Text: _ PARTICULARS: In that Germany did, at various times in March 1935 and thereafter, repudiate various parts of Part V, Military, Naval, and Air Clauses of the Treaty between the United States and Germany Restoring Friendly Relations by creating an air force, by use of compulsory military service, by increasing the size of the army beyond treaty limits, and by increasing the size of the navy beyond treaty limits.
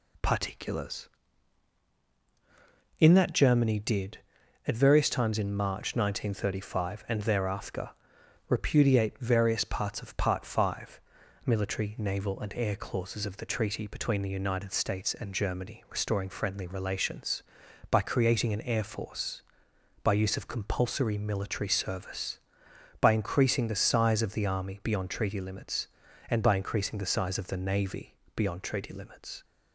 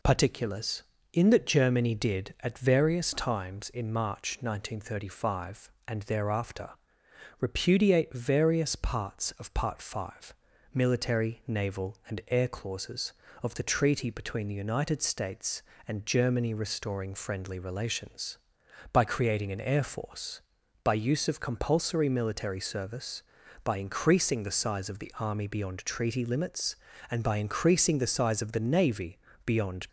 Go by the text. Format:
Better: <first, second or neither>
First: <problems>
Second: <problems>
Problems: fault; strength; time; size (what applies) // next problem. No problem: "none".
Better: first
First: pauses between "navy" and "beyond"; slight; at 28.1 s; 0.18 s long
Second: pauses between "navy" and "beyond"; slight; at 29.1 s; 0.24 s long // stops before "treaty limits"; at 29.8 s